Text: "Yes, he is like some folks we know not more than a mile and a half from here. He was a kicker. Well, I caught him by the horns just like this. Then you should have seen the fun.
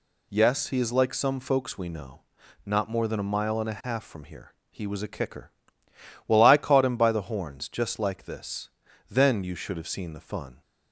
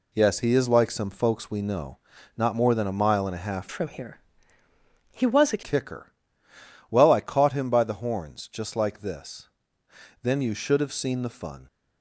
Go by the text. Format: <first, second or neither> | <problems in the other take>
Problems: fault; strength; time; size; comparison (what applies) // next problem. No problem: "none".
first | pauses between "know" and "not"; at 1.9 s; 0.40 s long; noticeable in the first // changes voice from "from" to "a"; from 3.7 to 5.6 s; 1.9 s long